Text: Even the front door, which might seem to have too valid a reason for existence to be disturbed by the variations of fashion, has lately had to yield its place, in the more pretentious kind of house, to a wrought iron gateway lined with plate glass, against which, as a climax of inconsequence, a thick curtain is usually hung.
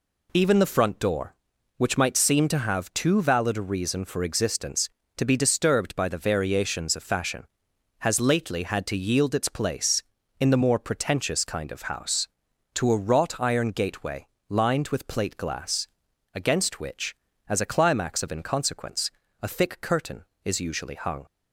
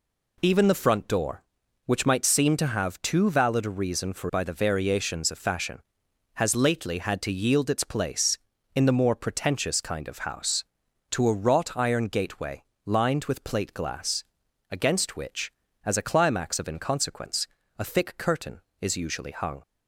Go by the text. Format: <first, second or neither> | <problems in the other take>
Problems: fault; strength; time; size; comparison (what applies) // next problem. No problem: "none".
first | skips "existence to be disturbed"; at 4.3 s // pauses between "gateway" and "lined"; slight; at 12.6 s; 0.22 s long; slight in the first